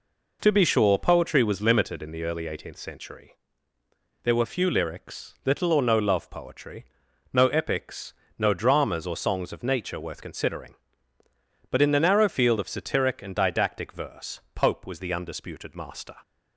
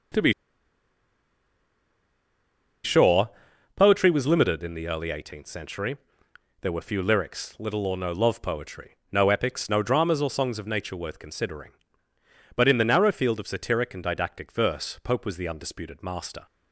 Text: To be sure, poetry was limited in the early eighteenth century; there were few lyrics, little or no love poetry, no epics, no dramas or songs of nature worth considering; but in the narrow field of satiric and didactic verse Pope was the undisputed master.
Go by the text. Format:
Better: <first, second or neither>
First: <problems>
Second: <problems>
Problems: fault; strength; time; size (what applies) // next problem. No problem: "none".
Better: first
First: none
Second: starts louder than the rest; until 4.1 s; 6.5 dB // pauses between "be" and "sure"; strong; at 0.3 s; 2.5 s long